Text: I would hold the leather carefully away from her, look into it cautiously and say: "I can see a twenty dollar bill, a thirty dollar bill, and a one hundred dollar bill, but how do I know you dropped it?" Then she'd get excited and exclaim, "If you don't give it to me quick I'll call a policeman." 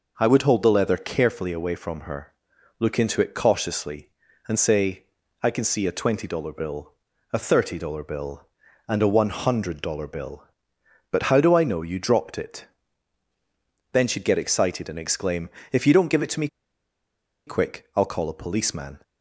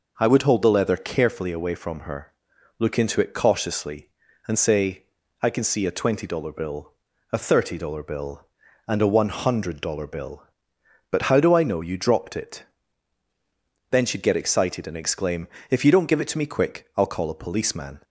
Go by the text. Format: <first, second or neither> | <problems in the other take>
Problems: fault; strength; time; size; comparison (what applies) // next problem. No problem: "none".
second | pauses between "me" and "quick"; at 16.4 s; 0.99 s long